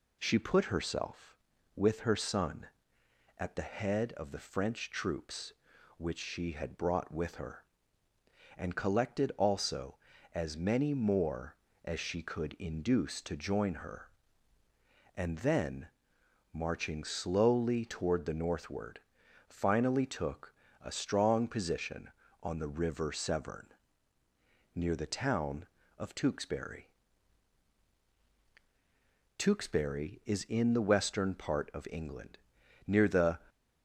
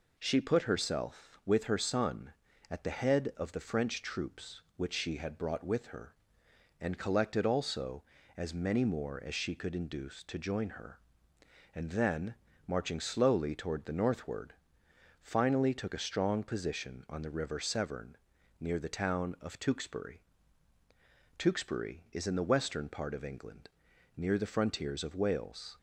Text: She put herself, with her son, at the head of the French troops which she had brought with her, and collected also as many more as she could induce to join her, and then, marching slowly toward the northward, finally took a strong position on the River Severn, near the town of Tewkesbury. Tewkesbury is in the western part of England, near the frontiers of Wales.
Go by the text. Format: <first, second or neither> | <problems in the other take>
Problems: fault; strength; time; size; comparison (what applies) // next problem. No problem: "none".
second | pauses between "took" and "a"; slight; at 20.5 s; 0.28 s long // stops before "frontiers of Wales"; at 33.4 s